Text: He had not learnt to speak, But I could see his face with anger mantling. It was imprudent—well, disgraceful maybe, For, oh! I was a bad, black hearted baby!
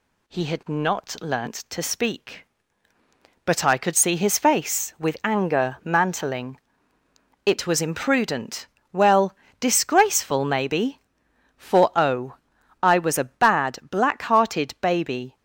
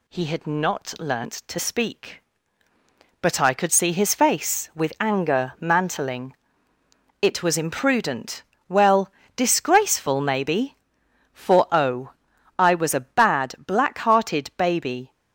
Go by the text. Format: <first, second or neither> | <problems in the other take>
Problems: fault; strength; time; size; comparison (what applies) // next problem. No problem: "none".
neither | none